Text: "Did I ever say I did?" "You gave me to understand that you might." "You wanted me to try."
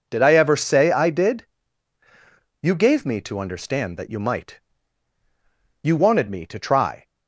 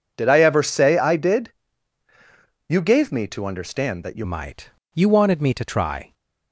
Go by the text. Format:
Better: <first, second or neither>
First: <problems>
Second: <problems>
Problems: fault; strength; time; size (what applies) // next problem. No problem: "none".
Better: first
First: none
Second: changes voice at "might"; from 4.2 s on; 1.9 s long